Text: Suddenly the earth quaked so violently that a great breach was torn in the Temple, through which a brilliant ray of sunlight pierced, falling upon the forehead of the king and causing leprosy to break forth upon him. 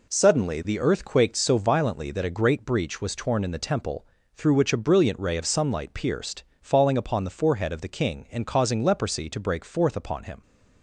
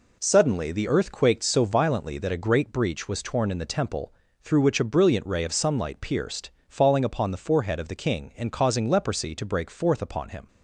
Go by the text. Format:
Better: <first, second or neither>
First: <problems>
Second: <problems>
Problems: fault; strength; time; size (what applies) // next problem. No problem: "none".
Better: neither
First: none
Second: none